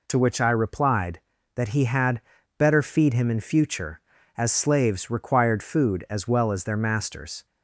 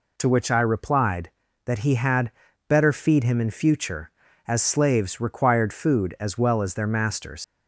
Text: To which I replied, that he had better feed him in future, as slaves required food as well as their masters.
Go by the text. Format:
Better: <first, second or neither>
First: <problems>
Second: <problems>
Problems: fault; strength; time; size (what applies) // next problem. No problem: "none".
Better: first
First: pauses between "had" and "better"; slight; at 2.2 s; 0.36 s long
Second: pauses between "had" and "better"; slight; at 2.3 s; 0.36 s long // leaves "masters" unfinished; at 7.4 s; 115 ms